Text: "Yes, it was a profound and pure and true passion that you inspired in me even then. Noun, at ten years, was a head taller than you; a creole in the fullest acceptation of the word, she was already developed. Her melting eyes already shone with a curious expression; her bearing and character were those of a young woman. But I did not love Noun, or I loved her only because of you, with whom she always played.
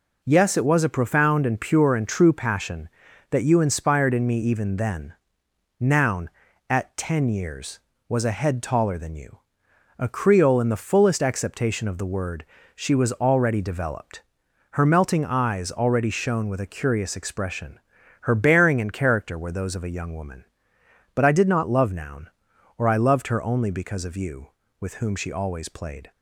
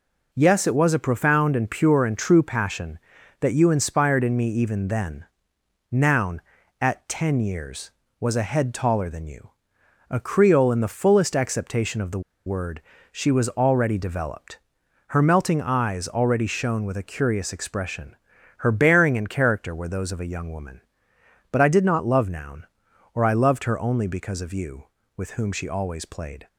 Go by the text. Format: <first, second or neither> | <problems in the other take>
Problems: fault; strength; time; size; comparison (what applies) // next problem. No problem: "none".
first | pauses between "the" and "word"; slight; at 12.1 s; 0.26 s long